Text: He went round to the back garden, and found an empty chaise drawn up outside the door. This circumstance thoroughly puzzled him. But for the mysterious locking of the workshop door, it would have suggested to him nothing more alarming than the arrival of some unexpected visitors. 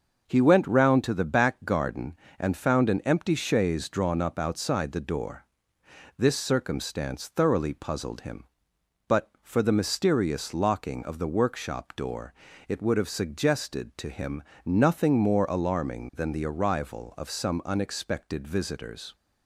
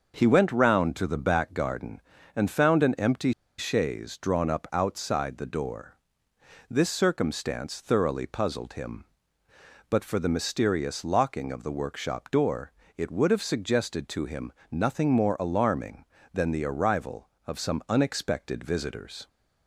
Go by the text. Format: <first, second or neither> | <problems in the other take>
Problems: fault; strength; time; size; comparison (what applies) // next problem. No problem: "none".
first | starts louder than the rest; noticeable; until 1.1 s; 6 dB; also in the first // pauses between "empty" and "chaise"; slight; at 3.3 s; 0.25 s long // pauses between "him" and "nothing"; slight; at 14.5 s; 0.18 s long; slight in the first